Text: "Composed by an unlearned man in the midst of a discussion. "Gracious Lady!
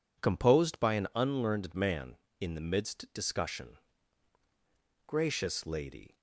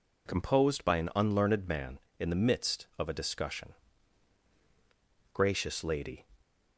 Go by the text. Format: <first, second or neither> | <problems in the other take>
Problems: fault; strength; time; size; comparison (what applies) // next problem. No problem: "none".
second | skips "of a"; at 3.0 s